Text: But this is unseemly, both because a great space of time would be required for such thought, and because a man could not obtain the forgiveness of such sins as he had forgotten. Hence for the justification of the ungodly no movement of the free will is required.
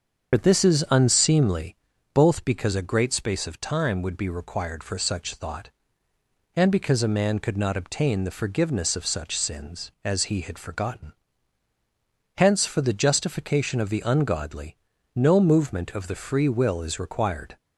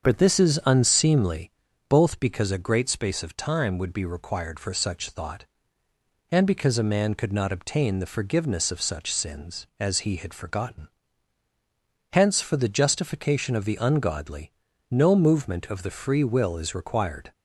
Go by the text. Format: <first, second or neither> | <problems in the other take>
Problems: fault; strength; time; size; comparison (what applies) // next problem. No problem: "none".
second | loses the start of "But"; at 0.3 s; 45 ms // starts louder than the rest; until 1.3 s; 7 dB; also in the second // pauses between "ungodly" and "no"; at 14.7 s; 0.38 s long; also in the second